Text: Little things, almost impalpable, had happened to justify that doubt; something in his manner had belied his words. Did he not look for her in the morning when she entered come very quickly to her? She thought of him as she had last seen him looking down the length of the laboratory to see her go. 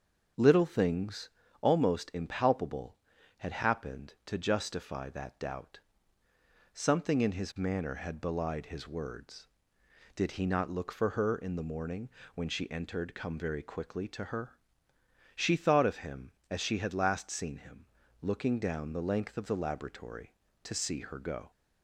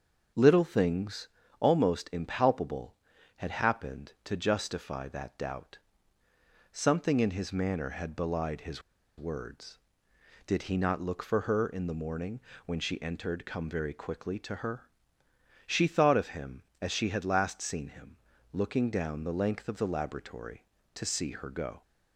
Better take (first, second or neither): first